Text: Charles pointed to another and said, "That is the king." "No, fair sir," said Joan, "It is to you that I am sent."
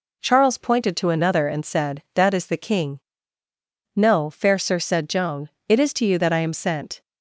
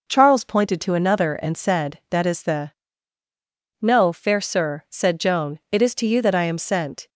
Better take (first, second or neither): first